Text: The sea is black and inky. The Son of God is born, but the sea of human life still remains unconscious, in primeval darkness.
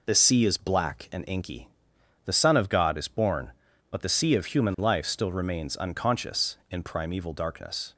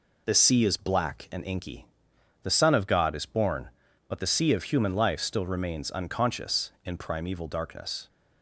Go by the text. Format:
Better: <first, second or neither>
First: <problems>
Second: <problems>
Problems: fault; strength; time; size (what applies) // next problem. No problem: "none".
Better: neither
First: none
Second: none